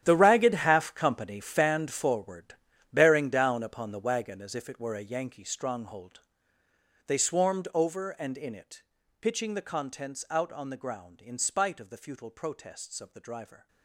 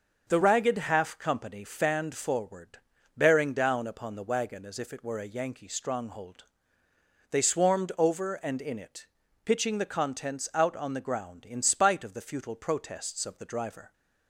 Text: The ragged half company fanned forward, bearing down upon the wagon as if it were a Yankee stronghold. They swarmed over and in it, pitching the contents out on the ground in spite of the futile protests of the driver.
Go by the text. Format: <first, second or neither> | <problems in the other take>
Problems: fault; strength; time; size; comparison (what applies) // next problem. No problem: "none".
second | gets quieter; strong; throughout; 15.5 dB // starts louder than the rest; strong; until 1.0 s; 11 dB; also in the second